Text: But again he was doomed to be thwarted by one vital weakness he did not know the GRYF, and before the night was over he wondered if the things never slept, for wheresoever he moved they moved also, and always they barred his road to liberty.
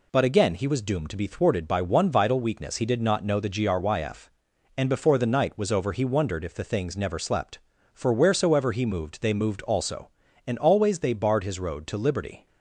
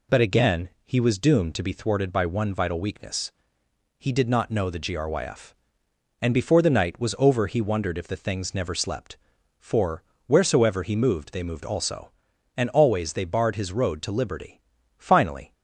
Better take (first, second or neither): first